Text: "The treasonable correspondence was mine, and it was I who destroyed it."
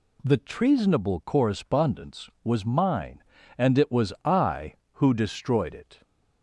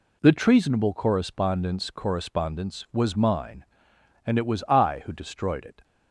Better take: first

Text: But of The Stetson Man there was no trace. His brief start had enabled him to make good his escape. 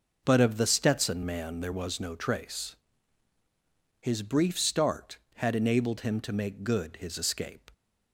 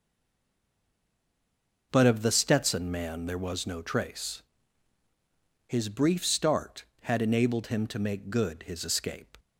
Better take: first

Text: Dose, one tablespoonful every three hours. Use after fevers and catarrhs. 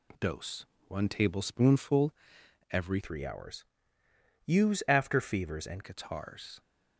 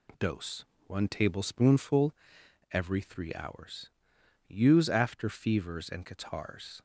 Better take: second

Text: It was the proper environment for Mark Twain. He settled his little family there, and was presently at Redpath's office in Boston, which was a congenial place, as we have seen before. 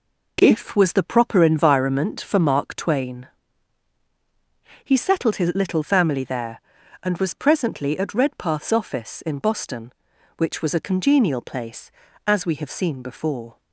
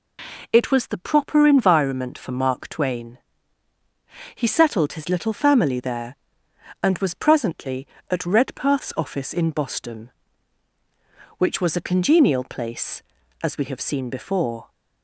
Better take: second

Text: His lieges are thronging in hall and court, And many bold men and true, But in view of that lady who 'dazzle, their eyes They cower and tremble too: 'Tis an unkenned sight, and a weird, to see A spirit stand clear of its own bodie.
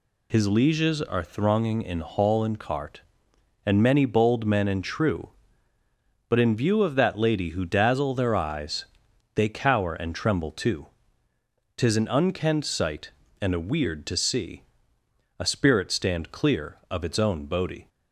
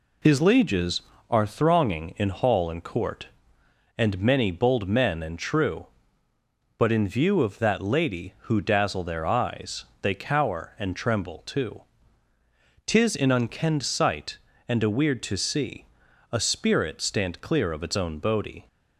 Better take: second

